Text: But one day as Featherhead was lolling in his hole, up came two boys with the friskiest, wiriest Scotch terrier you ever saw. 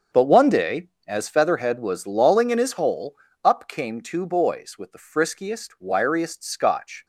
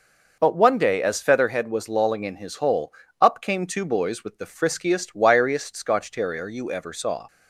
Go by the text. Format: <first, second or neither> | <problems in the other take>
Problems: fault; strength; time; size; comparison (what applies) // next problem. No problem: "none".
second | starts louder than the rest; until 1.3 s; 6.5 dB // stops before "terrier you ever saw"; at 7.0 s